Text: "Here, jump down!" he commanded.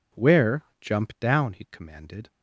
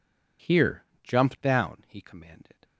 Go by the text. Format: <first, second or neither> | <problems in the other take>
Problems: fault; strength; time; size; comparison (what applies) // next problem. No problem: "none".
second | says "Where" for "Here"; at 0.1 s